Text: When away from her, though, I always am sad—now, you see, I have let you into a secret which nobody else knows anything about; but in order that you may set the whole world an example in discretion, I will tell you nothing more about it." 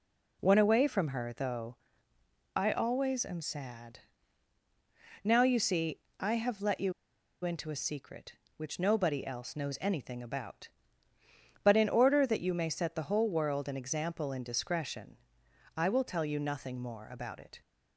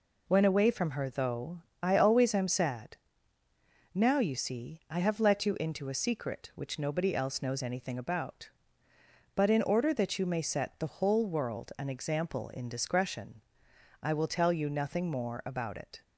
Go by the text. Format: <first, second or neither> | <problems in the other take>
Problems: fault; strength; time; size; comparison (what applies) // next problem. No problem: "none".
second | pauses between "you" and "into"; noticeable; at 6.9 s; 0.51 s long